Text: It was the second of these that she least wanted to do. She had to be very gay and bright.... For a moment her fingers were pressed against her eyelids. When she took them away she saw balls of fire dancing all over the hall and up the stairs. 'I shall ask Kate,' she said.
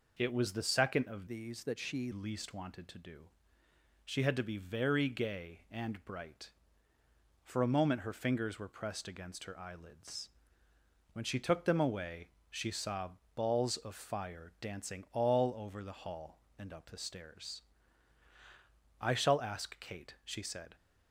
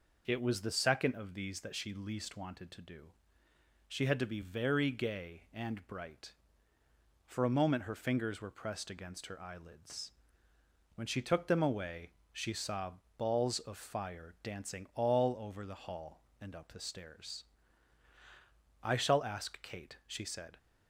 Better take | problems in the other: second | changes voice from "these" to "she"; from 1.2 to 2.1 s; 0.9 s long // pauses between "away" and "she"; slight; at 12.2 s; 0.22 s long; slight in the second // pauses between "saw" and "balls"; slight; at 13.0 s; 0.26 s long; slight in the second

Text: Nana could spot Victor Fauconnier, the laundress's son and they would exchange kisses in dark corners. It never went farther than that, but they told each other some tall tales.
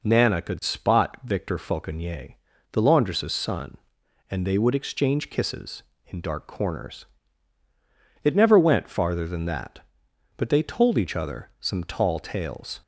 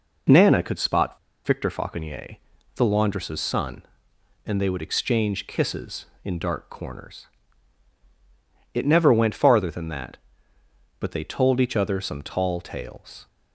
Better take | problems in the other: first | pauses between "spot" and "Victor"; slight; at 1.1 s; 0.26 s long

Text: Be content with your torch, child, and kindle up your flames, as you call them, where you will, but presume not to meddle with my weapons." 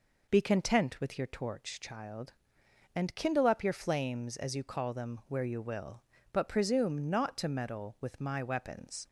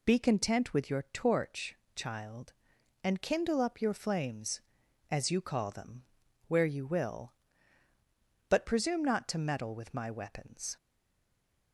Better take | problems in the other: first | stays silent after the last word; slight; from 10.7 s on; 1.0 s long

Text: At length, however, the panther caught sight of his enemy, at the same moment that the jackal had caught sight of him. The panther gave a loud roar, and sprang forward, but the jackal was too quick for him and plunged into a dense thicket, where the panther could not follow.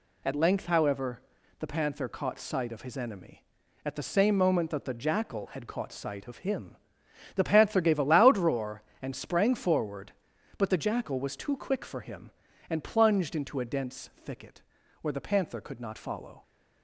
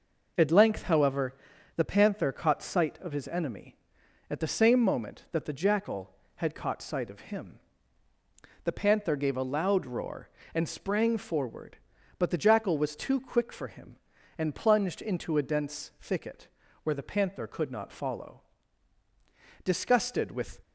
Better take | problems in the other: first | goes on to say "Disgusted with"; noticeable; from 19.6 s on; 0.96 s long

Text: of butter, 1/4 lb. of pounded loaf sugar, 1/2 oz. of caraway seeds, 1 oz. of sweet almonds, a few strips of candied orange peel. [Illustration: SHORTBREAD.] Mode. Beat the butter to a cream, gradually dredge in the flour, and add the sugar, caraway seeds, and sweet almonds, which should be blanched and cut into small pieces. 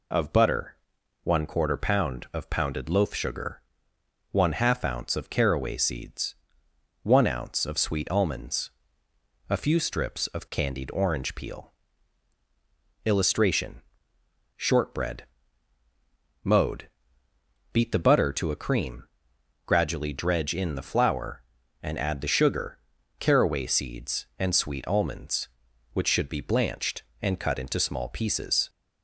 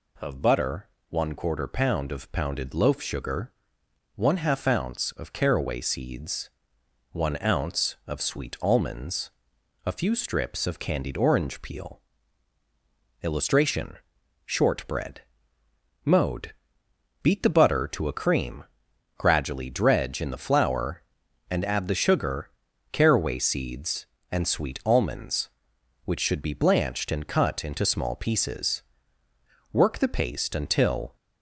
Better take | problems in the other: first | goes on to say "Work the paste until"; from 29.7 s on; 1.4 s long

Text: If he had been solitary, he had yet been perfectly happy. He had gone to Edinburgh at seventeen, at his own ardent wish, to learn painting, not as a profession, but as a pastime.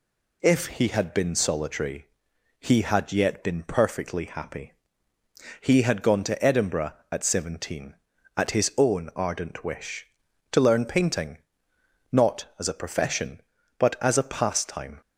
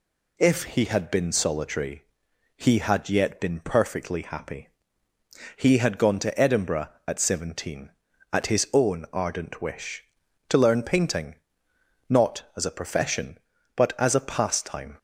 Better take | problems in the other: neither | none

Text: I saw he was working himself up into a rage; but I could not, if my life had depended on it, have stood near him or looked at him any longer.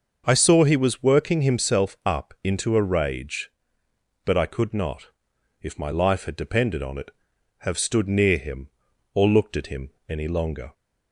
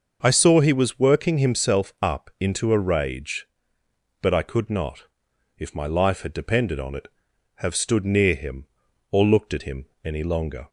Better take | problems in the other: neither | starts louder than the rest; the same in both // pauses between "him" and "any"; slight; the same in both

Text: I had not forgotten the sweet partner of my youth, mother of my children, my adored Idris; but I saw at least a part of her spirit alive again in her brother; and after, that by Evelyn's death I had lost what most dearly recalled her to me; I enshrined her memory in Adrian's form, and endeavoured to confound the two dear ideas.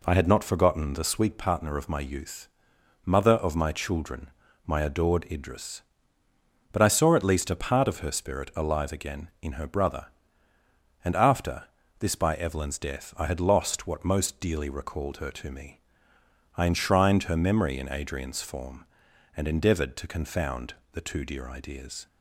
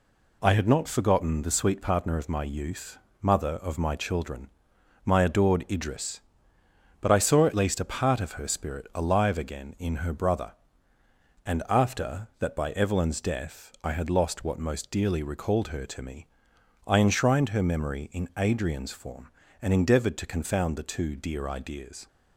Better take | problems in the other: second | says "this" for "that"; at 12.0 s // pauses between "confound" and "the"; slight; at 20.7 s; 0.16 s long

